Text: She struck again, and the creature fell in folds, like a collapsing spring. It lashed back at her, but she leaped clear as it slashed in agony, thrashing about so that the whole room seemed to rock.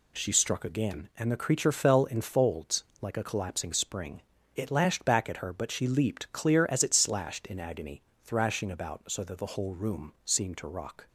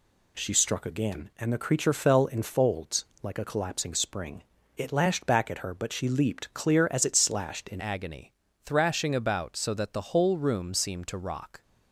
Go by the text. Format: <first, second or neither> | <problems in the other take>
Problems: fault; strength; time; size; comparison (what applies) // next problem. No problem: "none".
first | changes voice at "agony"; from 7.7 s on; 3.9 s long